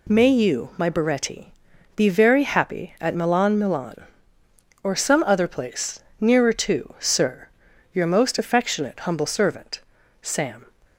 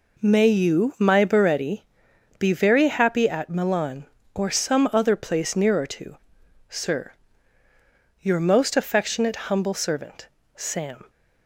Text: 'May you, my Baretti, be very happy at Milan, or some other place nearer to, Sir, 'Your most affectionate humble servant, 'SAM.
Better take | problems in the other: second | says "Milan" twice; at 3.5 s // pauses between "place" and "nearer"; slight; at 6.0 s; 0.20 s long

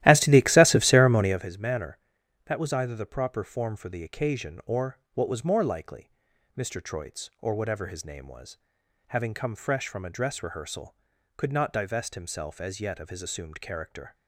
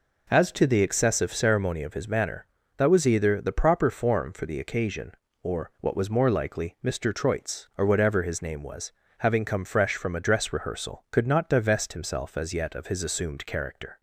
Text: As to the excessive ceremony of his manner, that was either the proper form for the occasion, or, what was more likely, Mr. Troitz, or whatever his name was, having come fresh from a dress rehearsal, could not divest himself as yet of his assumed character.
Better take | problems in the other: second | starts louder than the rest; strong; until 1.5 s; 14 dB

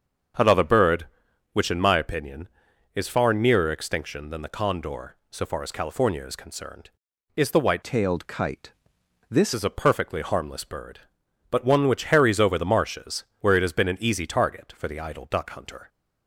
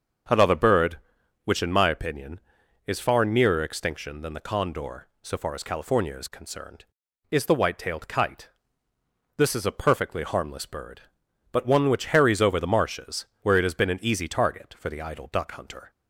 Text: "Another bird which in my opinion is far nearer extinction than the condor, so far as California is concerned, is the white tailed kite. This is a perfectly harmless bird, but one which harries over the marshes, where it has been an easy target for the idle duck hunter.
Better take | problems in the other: second | starts louder than the rest; until 1.8 s; 7 dB; also in the second // changes voice from "tailed" to "This"; from 7.8 to 9.5 s; 1.7 s long

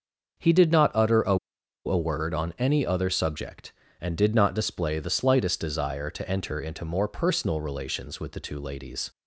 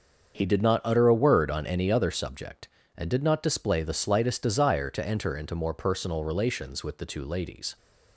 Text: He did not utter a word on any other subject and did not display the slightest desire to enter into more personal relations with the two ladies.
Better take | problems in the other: second | starts louder than the rest; until 1.8 s; 6 dB; also in the second // says "a" twice; at 1.8 s

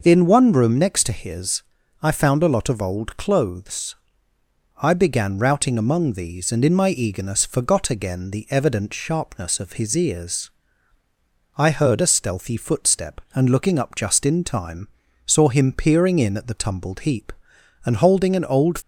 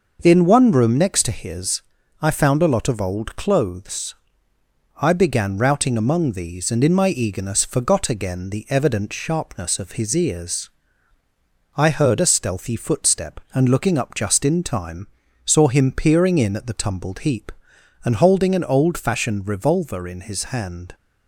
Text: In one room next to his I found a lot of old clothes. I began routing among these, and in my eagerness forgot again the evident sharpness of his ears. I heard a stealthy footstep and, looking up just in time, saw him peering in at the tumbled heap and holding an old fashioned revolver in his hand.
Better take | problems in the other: second | pauses between "his" and "I"; at 1.6 s; 0.40 s long; also in the second // stops before "fashioned revolver in his hand"; at 18.8 s

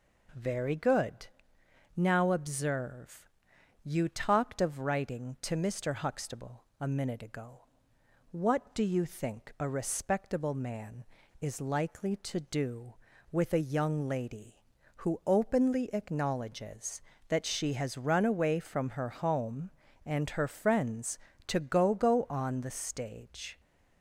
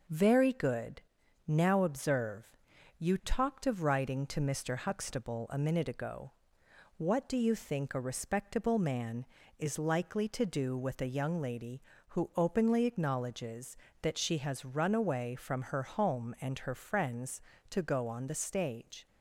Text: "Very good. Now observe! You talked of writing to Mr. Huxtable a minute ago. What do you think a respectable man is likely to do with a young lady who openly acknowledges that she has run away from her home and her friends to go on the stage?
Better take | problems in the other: second | pauses between "Huxtable" and "a"; slight; at 6.6 s; 0.18 s long // says "go" twice; at 21.9 s

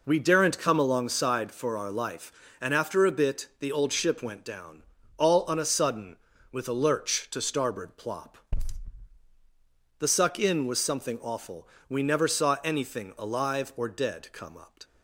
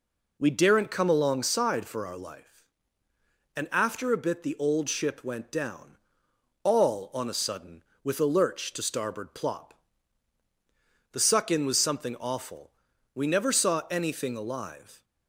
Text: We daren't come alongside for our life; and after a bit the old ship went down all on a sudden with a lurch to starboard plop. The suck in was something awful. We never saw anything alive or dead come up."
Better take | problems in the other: first | pauses between "down" and "all"; noticeable; at 5.9 s; 0.66 s long; slight in the first // stops before "or dead come up"; at 15.0 s

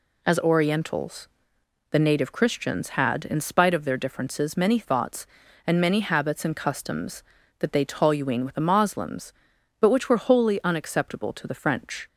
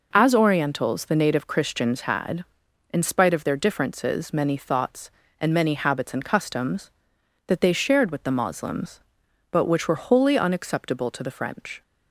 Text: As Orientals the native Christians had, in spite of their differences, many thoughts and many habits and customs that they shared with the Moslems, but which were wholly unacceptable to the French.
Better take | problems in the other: second | pauses between "Orientals" and "the"; noticeable; at 1.2 s; 0.62 s long // says "toluene" for "shared"; at 7.8 s

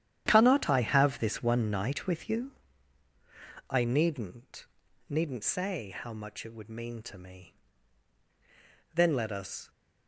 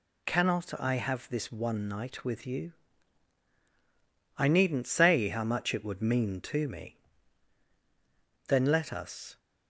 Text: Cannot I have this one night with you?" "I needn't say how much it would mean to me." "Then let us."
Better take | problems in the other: second | starts louder than the rest; strong; until 1.2 s; 10.5 dB // says "needn't" twice; at 5.0 s

